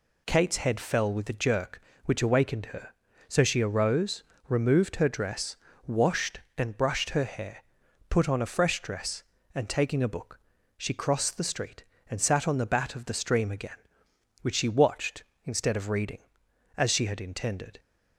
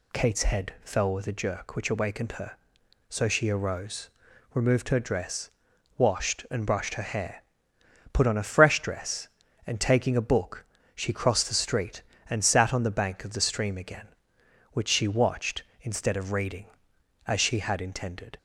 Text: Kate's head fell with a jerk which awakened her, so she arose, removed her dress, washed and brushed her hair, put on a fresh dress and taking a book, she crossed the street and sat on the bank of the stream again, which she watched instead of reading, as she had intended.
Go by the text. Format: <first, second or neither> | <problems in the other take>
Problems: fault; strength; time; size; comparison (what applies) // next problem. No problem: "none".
second | says "bat" for "bank"; at 12.6 s